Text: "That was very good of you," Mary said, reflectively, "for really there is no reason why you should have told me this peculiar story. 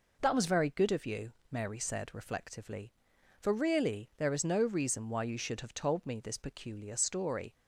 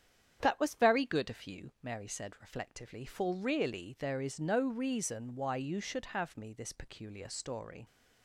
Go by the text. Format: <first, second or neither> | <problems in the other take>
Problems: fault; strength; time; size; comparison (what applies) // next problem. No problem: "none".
first | starts louder than the rest; strong; until 1.4 s; 8.5 dB // skips "told"; at 6.3 s